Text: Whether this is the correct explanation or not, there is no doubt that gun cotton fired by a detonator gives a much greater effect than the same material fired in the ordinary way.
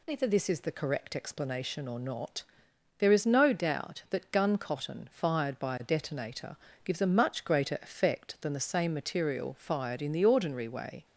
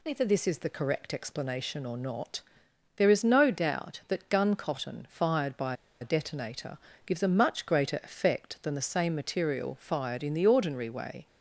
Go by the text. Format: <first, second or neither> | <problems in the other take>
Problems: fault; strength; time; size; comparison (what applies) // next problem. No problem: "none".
first | pauses between "by" and "a"; slight; at 5.7 s; 0.25 s long // pauses between "detonator" and "gives"; slight; at 6.7 s; 0.28 s long; slight in the first